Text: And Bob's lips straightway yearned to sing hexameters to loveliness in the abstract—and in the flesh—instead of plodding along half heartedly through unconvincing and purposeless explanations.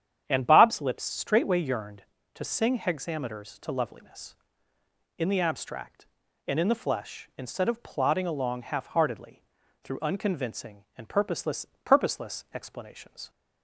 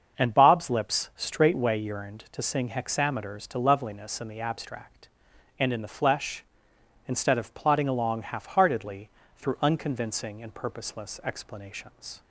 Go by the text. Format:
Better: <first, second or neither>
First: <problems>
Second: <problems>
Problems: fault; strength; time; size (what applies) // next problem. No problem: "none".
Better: second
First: starts louder than the rest; strong; until 1.2 s; 9 dB // pauses between "heartedly" and "through"; at 9.4 s; 0.38 s long // says "purposeless" twice; at 11.8 s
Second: starts louder than the rest; until 1.2 s; 6.5 dB // pauses between "heartedly" and "through"; slight; at 9.0 s; 0.28 s long